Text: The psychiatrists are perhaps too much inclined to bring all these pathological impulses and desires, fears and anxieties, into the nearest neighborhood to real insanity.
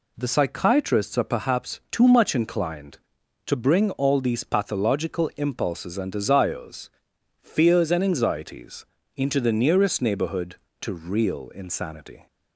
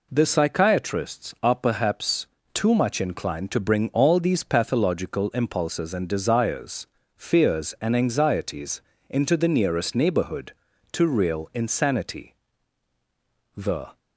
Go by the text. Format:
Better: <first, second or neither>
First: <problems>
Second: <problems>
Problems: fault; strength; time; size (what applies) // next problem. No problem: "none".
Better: first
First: none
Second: pauses between "perhaps" and "too"; slight; at 2.2 s; 0.28 s long // goes on to say "The"; slight; from 13.5 s on; 0.44 s long